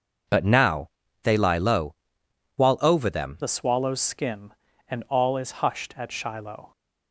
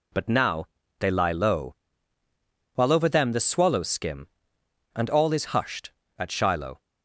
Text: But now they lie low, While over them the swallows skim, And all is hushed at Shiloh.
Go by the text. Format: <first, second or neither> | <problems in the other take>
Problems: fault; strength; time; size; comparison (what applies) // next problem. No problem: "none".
second | pauses between "now" and "they"; slight; at 0.8 s; 0.34 s long; slight in the second // changes voice at "the"; from 3.4 s on; 3.3 s long